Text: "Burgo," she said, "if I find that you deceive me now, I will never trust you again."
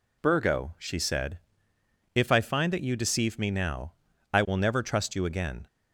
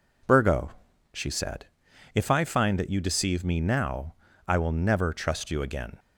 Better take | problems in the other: neither | none

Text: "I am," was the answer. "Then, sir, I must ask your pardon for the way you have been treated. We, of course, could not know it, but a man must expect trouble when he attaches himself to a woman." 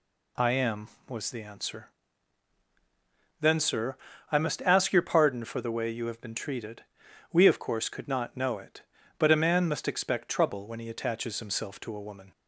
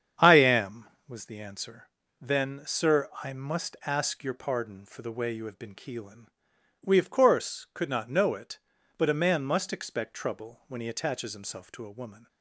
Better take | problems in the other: first | starts louder than the rest; strong; until 1.3 s; 8 dB // says "keelin" for "treated"; at 5.7 s

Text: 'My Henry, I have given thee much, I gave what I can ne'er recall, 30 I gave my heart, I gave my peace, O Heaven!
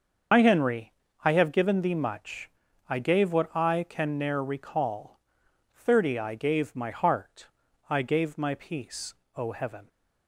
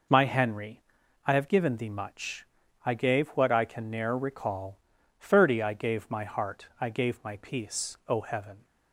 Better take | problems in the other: second | loses the start of "My"; at 0.3 s; 55 ms // starts louder than the rest; until 1.6 s; 6.5 dB

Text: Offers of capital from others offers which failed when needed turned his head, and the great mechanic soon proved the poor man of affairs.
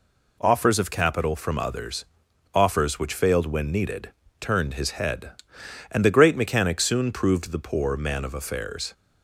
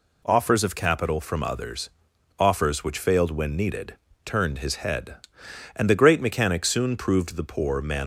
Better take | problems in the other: first | pauses between "others" and "offers"; noticeable; at 1.8 s; 0.48 s long; noticeable in the first // pauses between "needed" and "turned"; slight; at 3.9 s; 0.28 s long; slight in the first // stops before "of affairs"; at 8.0 s

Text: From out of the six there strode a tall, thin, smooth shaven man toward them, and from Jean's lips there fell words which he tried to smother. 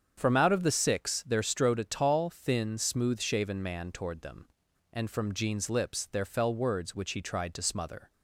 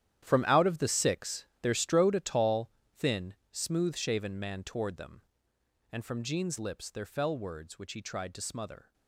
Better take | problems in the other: first | gets quieter; strong; throughout; 14 dB // starts louder than the rest; strong; until 1.2 s; 11 dB; strong in the first // pauses between "six" and "there"; slight; at 1.4 s; 0.16 s long

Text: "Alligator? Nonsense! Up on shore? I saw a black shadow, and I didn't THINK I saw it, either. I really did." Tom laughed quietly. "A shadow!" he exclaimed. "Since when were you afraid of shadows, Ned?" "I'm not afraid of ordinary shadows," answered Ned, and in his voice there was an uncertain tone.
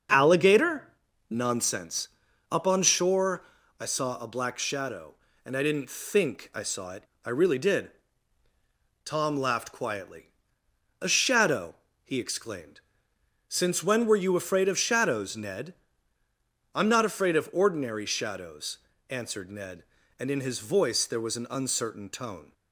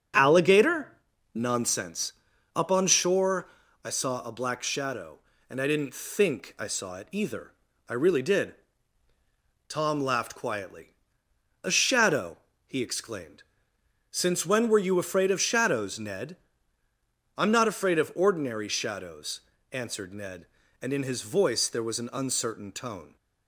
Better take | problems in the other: second | starts louder than the rest; until 1.5 s; 6.5 dB; strong in the second // skips "either"; at 7.1 s

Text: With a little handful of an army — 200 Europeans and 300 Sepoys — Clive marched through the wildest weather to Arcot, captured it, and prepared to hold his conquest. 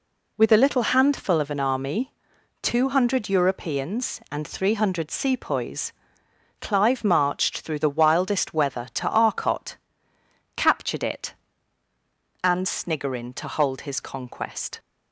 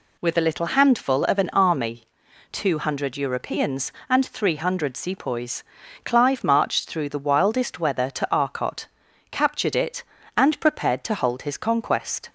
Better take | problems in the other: second | says "sniggerin" for "prepared"; at 12.6 s

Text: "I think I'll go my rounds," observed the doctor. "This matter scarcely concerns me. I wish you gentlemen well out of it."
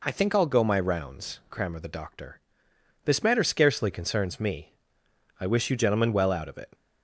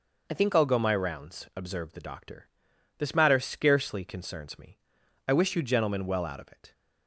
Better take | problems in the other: second | says "crammer" for "observed"; at 1.4 s

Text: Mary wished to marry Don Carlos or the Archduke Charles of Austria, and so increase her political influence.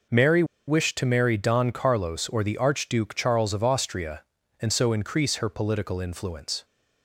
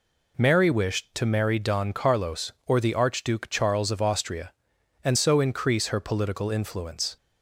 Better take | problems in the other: second | pauses between "Mary" and "wished"; slight; at 0.4 s; 0.23 s long

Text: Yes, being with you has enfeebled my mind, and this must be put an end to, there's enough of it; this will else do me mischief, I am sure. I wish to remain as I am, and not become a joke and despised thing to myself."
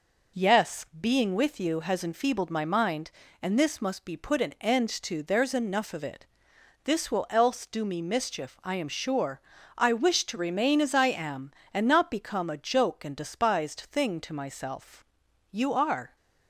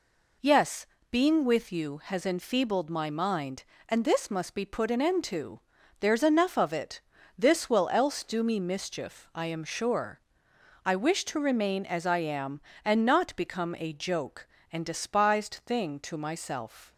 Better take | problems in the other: second | goes on to say "You are"; noticeable; from 15.5 s on; 0.64 s long

